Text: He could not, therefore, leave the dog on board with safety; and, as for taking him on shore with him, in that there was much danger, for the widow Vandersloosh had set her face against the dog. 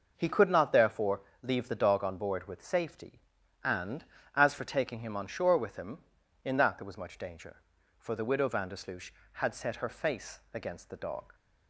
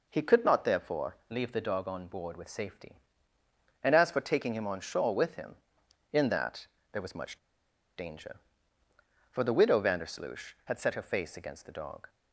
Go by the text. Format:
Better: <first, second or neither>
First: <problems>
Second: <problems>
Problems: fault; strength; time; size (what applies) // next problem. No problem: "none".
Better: first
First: none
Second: pauses between "that" and "there"; slight; at 6.6 s; 0.26 s long // pauses between "much" and "danger"; noticeable; at 7.3 s; 0.60 s long